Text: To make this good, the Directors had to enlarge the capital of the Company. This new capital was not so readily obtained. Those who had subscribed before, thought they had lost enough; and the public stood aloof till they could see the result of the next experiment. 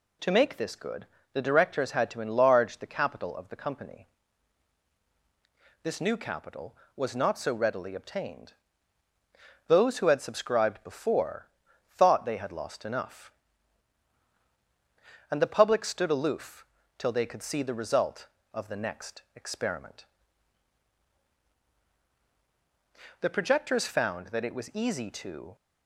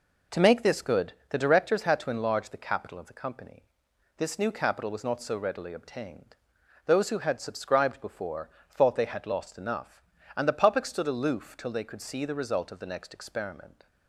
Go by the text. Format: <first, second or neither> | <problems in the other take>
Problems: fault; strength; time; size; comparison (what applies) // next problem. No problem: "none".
second | pauses between "aloof" and "till"; slight; at 16.6 s; 0.32 s long // goes on to say "The projectors found that it was easy to"; strong; from 23.2 s on; 2.3 s long